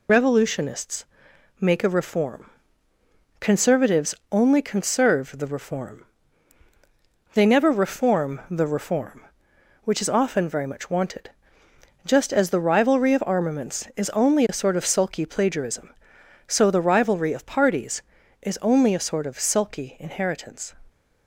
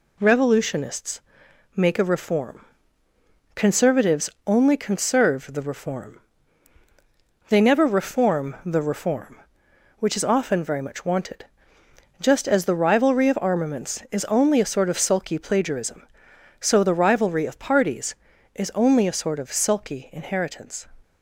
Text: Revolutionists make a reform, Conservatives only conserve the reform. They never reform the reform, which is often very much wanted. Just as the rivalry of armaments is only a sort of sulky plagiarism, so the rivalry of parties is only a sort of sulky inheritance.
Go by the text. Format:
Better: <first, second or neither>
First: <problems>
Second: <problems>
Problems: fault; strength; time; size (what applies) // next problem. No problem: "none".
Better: second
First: loses the start of "Revolutionists"; at 0.0 s; 55 ms // pauses between "Revolutionists" and "make"; noticeable; at 1.0 s; 0.56 s long // pauses between "Conservatives" and "only"; slight; at 4.1 s; 0.16 s long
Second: pauses between "Revolutionists" and "make"; noticeable; at 1.1 s; 0.56 s long // pauses between "Conservatives" and "only"; slight; at 4.3 s; 0.16 s long